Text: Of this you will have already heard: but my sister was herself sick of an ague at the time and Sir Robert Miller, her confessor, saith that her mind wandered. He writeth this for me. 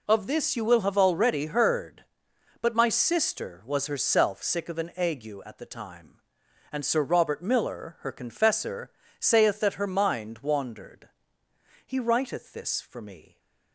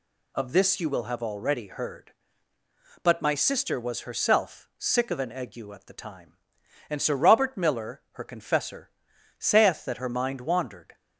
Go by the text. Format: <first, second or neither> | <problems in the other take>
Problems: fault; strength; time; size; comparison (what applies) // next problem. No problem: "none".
first | stops before "He writeth this for me"; at 10.9 s